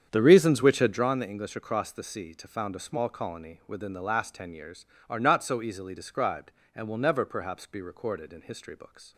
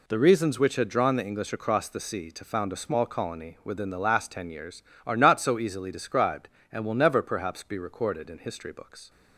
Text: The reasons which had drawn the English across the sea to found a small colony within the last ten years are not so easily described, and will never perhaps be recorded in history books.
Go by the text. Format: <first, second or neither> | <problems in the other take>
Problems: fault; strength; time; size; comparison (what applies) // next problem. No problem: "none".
second | starts louder than the rest; strong; until 1.1 s; 8 dB